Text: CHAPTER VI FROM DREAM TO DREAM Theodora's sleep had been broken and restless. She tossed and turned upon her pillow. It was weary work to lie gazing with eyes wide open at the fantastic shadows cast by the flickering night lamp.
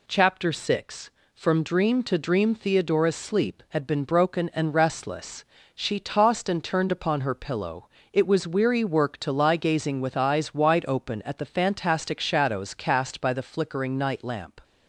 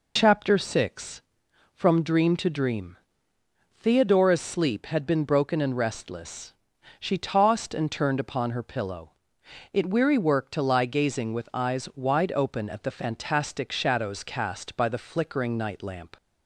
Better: first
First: none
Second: pauses between "DREAM" and "Theodora's"; noticeable; at 2.9 s; 0.80 s long // skips "was"; at 9.9 s

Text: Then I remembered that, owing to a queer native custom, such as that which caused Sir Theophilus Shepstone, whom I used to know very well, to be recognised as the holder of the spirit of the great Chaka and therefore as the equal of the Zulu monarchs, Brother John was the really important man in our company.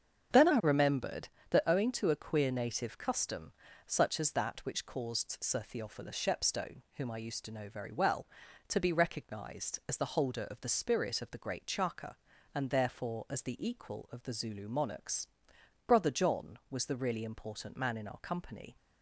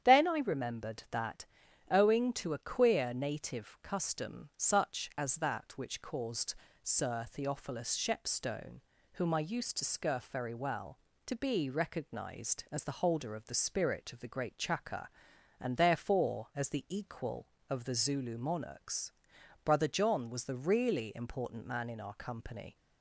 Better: first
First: starts louder than the rest; strong; until 1.5 s; 7.5 dB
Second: starts louder than the rest; strong; until 1.1 s; 9 dB // pauses between "caused" and "Sir"; slight; at 6.5 s; 0.30 s long // says "scurf" for "know"; at 9.8 s

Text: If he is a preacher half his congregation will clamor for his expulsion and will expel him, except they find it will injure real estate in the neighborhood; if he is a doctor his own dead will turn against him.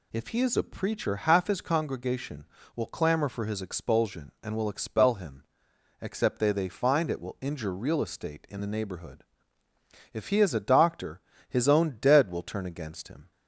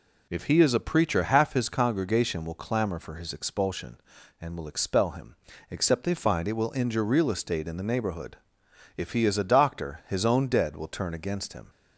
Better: second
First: says "they" twice; at 6.4 s // pauses between "doctor" and "his"; slight; at 11.1 s; 0.30 s long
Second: none

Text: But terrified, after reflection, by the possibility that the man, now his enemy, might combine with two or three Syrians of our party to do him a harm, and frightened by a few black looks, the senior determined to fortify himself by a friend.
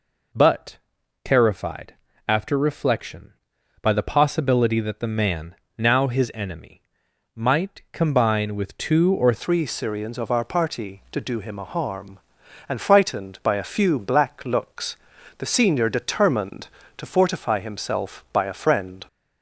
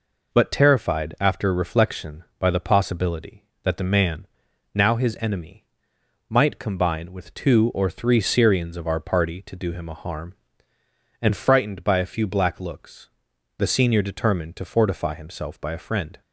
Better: second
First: pauses between "But" and "terrified"; noticeable; at 0.7 s; 0.46 s long // changes voice at "three"; from 9.3 s on; 9.7 s long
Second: none

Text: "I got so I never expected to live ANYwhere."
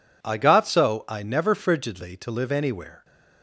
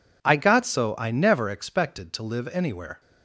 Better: second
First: says "frigidly" for "expected"; at 1.5 s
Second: none

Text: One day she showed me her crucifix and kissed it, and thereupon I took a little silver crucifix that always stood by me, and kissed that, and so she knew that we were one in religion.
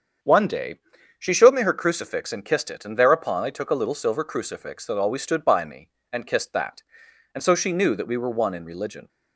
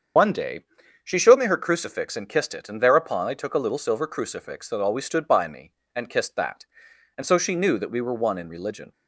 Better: first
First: starts louder than the rest; strong; until 1.6 s; 7.5 dB // pauses between "day" and "she"; at 0.7 s; 0.42 s long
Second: loses the start of "One"; at 0.1 s; 75 ms // starts louder than the rest; strong; until 1.5 s; 7.5 dB // pauses between "day" and "she"; at 0.6 s; 0.42 s long

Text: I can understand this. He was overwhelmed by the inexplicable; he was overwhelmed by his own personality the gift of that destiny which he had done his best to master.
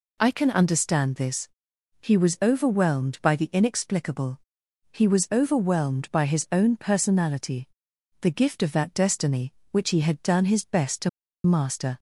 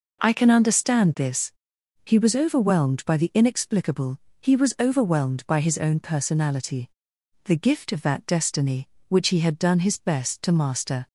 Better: second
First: pauses between "personality" and "the"; noticeable; at 7.6 s; 0.54 s long // pauses between "to" and "master"; slight; at 11.0 s; 0.35 s long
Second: pauses between "personality" and "the"; noticeable; at 6.8 s; 0.56 s long

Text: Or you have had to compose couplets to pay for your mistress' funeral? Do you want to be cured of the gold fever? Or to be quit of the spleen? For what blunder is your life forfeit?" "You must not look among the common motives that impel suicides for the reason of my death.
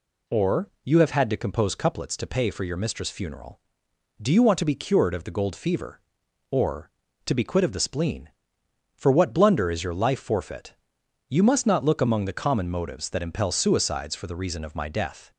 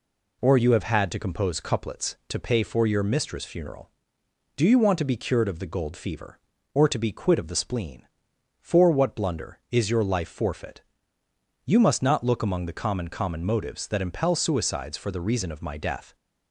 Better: first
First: none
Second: says "common" twice; at 13.0 s

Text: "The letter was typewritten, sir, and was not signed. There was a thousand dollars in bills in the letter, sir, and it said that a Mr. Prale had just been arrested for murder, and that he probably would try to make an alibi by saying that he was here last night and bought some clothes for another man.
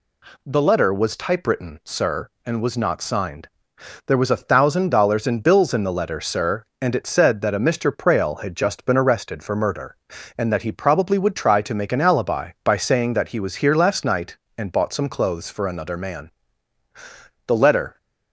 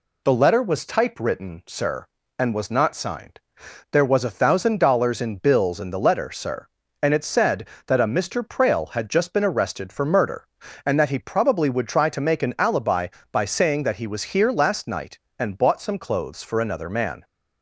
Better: second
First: goes on to say "The letter"; from 17.4 s on; 0.50 s long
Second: none

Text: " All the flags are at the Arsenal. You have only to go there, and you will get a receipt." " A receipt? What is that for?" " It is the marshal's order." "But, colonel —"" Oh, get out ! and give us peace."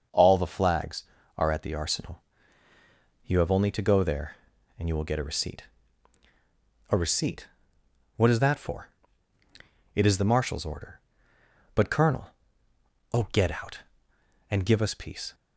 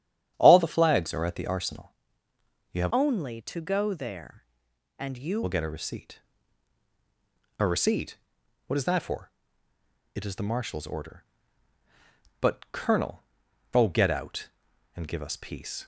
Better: first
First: starts louder than the rest; until 1.4 s; 6.5 dB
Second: starts louder than the rest; strong; until 1.3 s; 12.5 dB // changes voice from "only" to "you"; from 2.9 to 5.4 s; 2.5 s long

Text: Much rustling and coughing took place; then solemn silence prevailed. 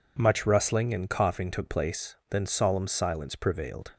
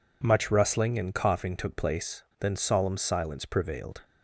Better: neither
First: none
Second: none

